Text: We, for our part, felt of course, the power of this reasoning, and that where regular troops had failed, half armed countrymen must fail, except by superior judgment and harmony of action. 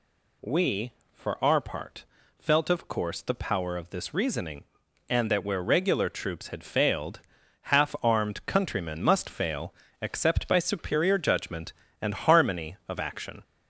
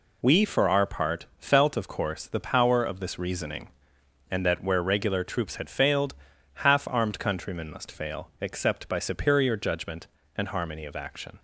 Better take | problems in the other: second | gets louder; slight; throughout; 3.5 dB

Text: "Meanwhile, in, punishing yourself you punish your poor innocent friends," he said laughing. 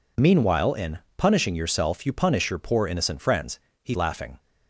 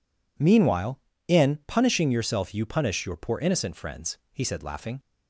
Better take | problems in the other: second | skips "said"; at 3.9 s

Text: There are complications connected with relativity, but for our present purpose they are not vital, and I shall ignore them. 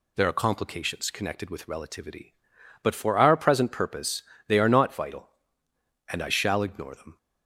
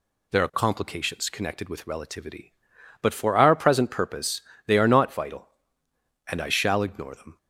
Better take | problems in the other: neither | pauses between "purpose" and "they"; slight; the same in both

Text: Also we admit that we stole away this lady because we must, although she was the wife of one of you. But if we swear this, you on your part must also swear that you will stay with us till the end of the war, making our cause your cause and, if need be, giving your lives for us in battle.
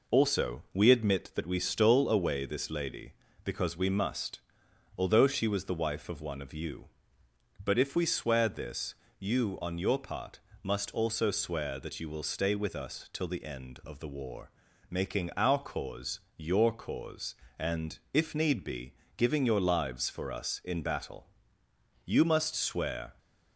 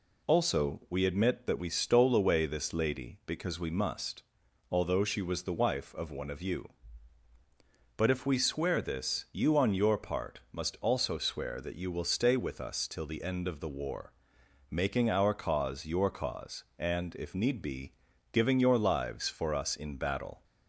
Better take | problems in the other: second | pauses between "part" and "must"; slight; at 10.3 s; 0.24 s long // pauses between "cause" and "your"; slight; at 16.1 s; 0.16 s long // goes on to say "You must swear"; noticeable; from 22.0 s on; 1.1 s long

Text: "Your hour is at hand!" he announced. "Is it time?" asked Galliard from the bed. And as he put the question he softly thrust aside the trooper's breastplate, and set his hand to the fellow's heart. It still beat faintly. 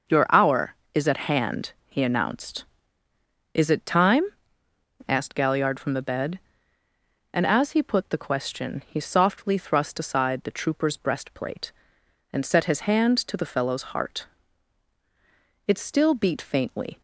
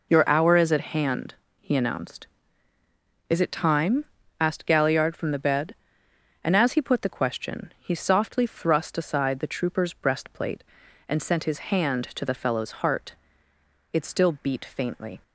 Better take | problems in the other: first | says "sent" for "set"; at 11.2 s

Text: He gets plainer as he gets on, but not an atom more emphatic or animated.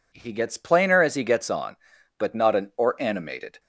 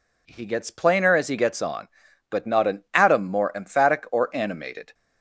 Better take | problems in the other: second | skips "atom more emphatic"; at 2.7 s

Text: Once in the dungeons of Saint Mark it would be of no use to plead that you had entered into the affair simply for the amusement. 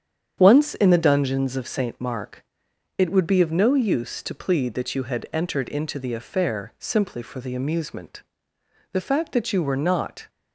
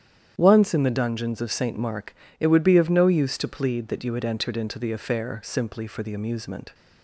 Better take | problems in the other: second | starts louder than the rest; strong; until 1.4 s; 8.5 dB; strong in the second // pauses between "Mark" and "it"; noticeable; at 2.4 s; 0.52 s long; slight in the second // goes on to say "The fact that you were not"; from 8.9 s on; 1.3 s long

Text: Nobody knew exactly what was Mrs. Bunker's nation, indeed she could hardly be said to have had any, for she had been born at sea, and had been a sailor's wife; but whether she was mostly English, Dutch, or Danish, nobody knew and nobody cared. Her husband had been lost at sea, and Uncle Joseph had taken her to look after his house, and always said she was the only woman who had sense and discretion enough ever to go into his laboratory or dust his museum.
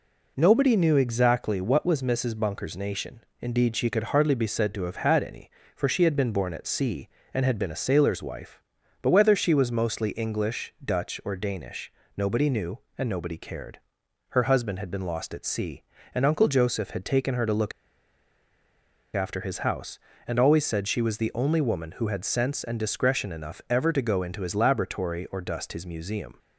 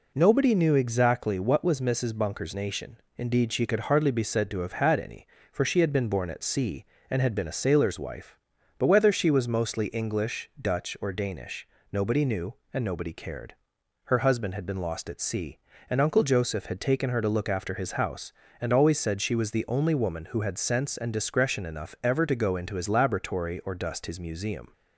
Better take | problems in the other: second | pauses between "look" and "after"; strong; at 17.7 s; 1.4 s long

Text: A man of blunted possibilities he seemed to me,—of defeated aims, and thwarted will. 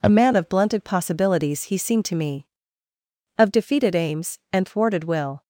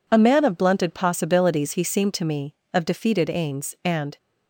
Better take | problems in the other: first | stops before "thwarted will"; at 4.1 s

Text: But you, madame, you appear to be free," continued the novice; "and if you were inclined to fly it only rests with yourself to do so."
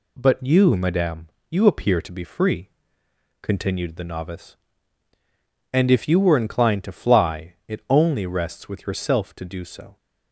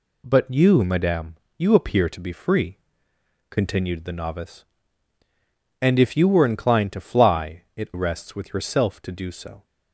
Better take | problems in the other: first | skips "only"; at 7.9 s

